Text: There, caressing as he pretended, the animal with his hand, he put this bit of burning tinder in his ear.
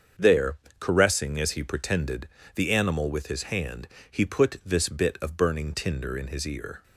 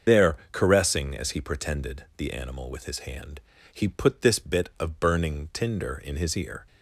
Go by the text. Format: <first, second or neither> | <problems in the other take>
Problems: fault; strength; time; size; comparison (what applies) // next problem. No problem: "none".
first | loses the start of "There"; at 0.0 s; 70 ms // starts louder than the rest; until 1.2 s; 6.5 dB; also in the first